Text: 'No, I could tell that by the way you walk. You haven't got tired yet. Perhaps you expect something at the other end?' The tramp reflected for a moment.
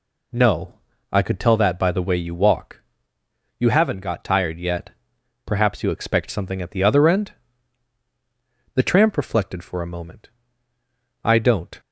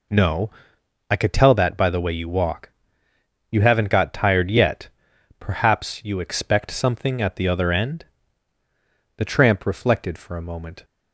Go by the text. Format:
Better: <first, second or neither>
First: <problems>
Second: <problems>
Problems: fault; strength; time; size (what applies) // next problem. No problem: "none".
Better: second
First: goes on to say "I don't"; from 11.2 s on; 0.56 s long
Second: none